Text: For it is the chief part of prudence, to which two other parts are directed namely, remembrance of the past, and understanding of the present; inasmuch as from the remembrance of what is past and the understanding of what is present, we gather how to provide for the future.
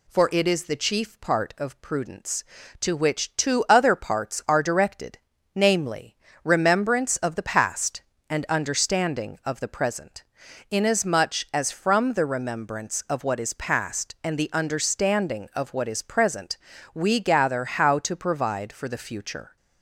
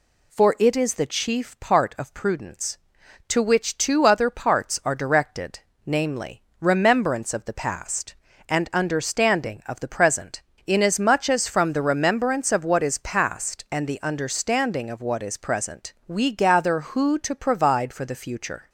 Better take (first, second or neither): first